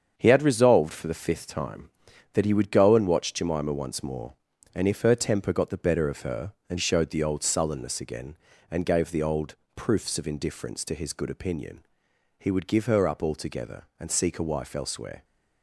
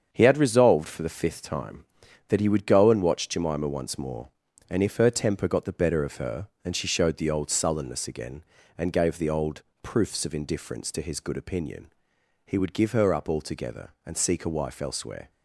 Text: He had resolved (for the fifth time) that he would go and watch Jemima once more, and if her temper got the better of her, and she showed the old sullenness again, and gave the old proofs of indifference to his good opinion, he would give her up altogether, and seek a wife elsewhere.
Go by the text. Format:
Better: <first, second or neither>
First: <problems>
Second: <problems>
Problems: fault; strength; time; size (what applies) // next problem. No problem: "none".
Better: second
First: starts louder than the rest; strong; until 1.2 s; 7 dB // skips "she"; at 6.7 s // pauses between "old" and "proofs"; slight; at 9.5 s; 0.20 s long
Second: starts louder than the rest; until 1.1 s; 7 dB // pauses between "old" and "proofs"; slight; at 9.6 s; 0.20 s long